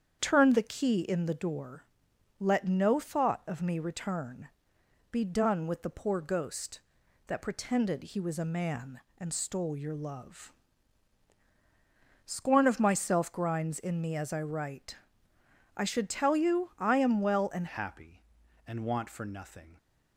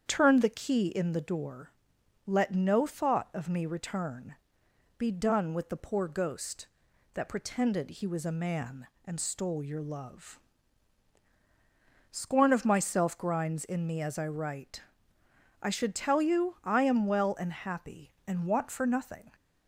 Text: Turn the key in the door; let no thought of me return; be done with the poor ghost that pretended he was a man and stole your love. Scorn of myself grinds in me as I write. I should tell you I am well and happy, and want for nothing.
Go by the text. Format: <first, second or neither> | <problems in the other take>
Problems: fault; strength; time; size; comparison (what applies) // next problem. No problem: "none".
second | starts louder than the rest; strong; until 1.2 s; 8 dB; strong in the second // changes voice at "happy"; from 17.6 s on; 2.1 s long